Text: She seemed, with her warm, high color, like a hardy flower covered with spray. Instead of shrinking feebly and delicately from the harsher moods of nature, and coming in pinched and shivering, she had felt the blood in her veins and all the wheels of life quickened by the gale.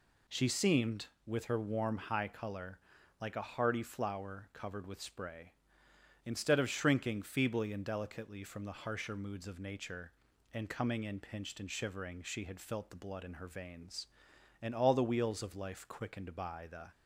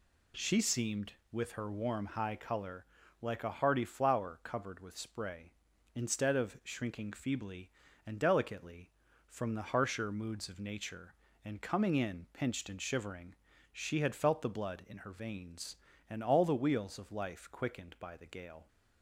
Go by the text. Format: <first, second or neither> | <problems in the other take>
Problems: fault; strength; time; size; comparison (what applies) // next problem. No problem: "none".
second | stops before "gale"; at 16.9 s